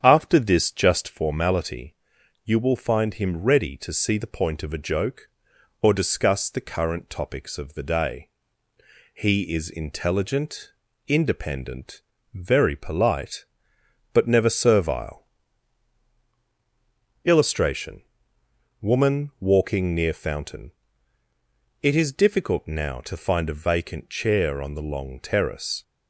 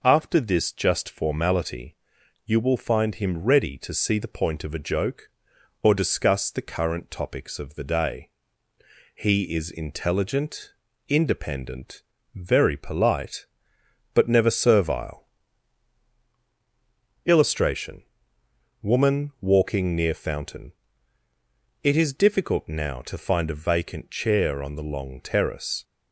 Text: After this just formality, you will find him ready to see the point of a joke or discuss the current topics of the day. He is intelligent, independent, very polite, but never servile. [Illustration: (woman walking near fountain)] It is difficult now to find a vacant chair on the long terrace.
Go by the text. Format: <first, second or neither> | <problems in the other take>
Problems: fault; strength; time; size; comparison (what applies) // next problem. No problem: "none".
second | starts louder than the rest; strong; until 1.1 s; 8 dB